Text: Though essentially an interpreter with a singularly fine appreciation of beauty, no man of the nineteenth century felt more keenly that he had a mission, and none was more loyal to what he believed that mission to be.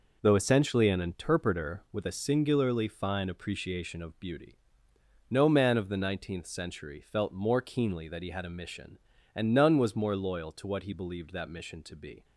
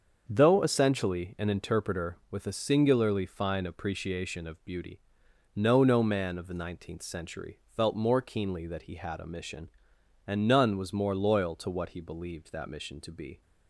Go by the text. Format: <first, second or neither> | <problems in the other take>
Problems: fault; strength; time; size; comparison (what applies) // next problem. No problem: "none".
first | starts louder than the rest; until 1.2 s; 6.5 dB // says "no" twice; at 5.8 s // pauses between "century" and "felt"; slight; at 7.5 s; 0.18 s long